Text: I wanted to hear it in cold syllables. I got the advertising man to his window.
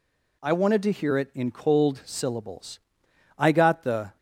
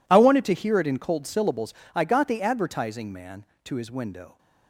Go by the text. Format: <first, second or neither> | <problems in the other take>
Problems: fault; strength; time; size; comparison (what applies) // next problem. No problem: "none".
second | stops before "advertising man to his window"; at 4.1 s